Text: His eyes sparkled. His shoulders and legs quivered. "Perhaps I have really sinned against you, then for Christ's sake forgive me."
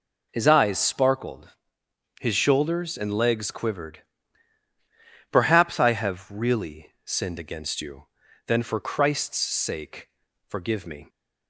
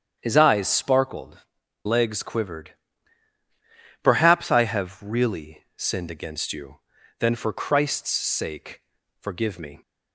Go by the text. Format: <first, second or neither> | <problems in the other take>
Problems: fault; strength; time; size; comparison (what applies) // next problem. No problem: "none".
first | starts louder than the rest; strong; until 1.2 s; 8.5 dB // skips "His shoulders and"; at 1.6 s // pauses between "sake" and "forgive"; at 8.8 s; 0.38 s long; also in the first